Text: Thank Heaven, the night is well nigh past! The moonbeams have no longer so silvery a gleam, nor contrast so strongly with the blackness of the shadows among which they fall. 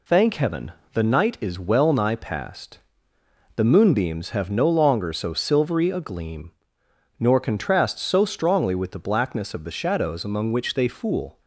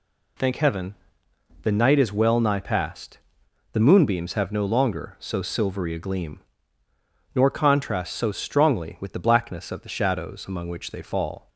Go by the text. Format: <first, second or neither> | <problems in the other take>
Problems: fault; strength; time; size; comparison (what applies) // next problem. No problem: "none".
second | says "fool" for "fall"; at 10.8 s